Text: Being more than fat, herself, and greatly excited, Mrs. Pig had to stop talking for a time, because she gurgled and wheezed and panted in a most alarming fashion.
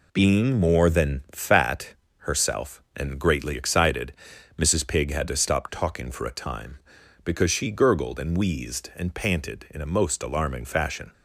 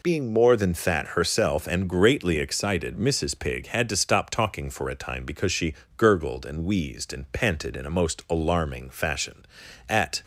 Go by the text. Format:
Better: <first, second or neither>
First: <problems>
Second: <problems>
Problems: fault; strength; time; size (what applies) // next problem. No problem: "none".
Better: first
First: none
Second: pauses between "she" and "gurgled"; slight; at 5.7 s; 0.24 s long // goes on to say "At"; slight; from 9.8 s on; 0.34 s long